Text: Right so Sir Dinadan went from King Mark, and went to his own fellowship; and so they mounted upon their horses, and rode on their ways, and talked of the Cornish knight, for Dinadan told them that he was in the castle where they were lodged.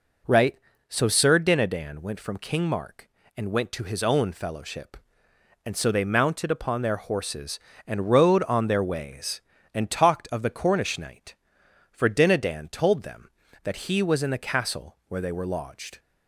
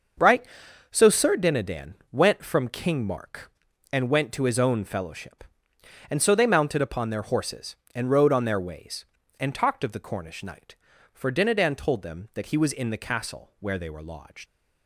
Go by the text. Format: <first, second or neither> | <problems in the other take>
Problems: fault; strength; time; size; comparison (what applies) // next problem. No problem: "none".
first | starts louder than the rest; until 1.6 s; 6.5 dB // pauses between "Dinadan" and "went"; slight; at 1.9 s; 0.18 s long // leaves "lodged" unfinished; at 14.4 s; 80 ms